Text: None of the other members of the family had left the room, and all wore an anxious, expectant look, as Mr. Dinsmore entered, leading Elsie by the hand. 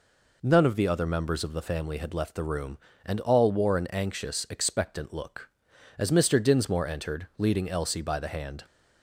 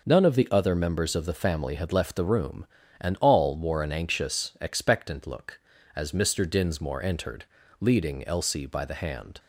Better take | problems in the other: neither | none

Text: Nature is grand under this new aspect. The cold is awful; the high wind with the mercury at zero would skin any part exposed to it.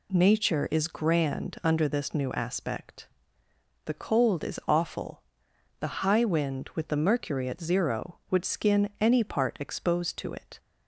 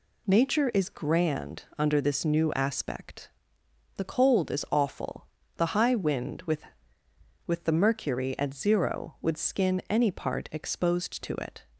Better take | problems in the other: first | says "with" twice; at 7.4 s

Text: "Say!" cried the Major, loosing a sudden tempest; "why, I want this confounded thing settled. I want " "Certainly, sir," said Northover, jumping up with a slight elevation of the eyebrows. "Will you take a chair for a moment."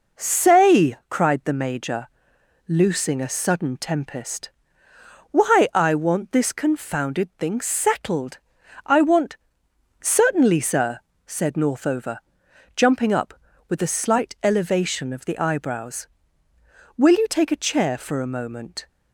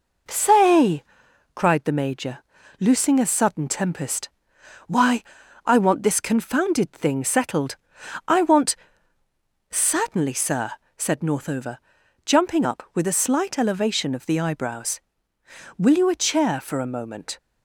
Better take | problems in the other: first | skips "take"; at 16.0 s

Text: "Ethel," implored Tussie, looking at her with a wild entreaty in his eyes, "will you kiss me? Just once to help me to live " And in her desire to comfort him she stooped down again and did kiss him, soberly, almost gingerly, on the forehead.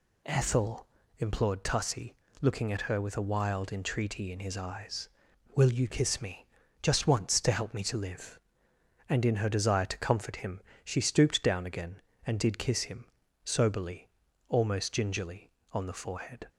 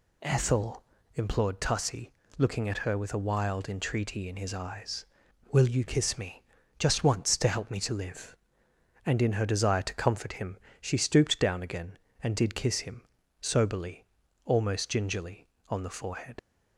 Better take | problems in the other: first | pauses between "him" and "she"; slight; at 10.5 s; 0.24 s long; slight in the first // leaves "forehead" unfinished; at 16.3 s; 55 ms

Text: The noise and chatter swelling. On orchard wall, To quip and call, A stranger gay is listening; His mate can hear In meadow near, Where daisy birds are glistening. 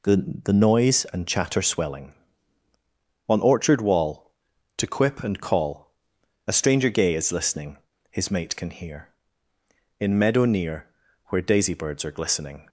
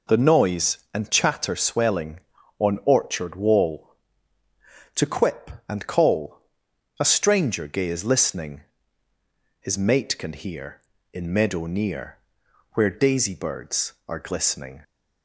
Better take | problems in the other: second | says "The" twice; at 0.4 s

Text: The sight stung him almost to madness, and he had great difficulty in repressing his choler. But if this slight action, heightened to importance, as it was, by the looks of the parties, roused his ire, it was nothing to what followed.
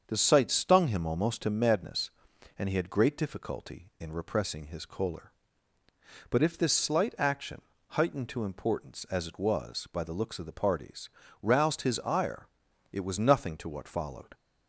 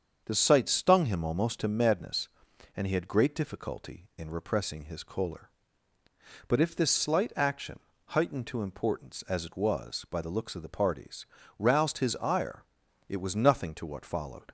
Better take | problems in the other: neither | starts louder than the rest; the same in both

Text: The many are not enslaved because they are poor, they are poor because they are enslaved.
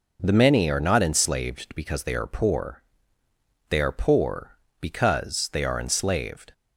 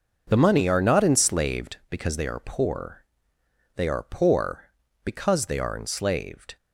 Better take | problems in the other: first | starts louder than the rest; noticeable; until 1.2 s; 6 dB // says "money" for "many"; at 0.3 s

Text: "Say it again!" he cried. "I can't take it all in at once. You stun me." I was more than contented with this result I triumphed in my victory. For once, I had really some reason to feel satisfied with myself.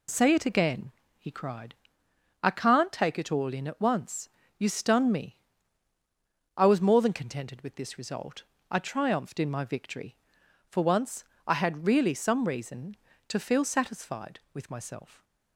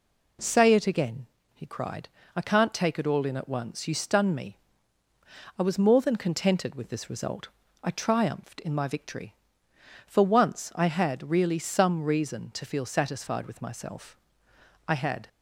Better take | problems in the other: first | pauses between "result" and "I"; slight; at 7.4 s; 0.36 s long; slight in the first // goes on to say "I had"; slight; from 14.8 s on; 0.40 s long

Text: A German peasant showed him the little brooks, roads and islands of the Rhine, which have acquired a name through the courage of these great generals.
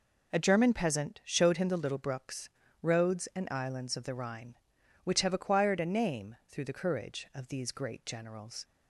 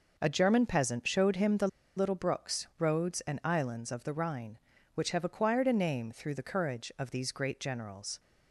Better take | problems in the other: first | pauses between "the" and "little"; slight; at 1.6 s; 0.29 s long

